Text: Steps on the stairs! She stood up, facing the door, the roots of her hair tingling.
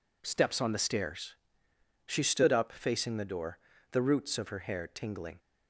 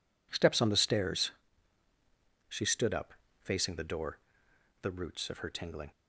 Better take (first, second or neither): first